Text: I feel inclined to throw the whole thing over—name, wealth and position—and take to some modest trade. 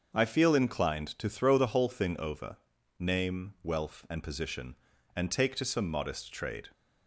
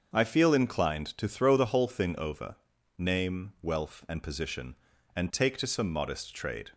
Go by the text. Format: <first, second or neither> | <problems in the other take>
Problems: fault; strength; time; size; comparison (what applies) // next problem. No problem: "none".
neither | starts louder than the rest; the same in both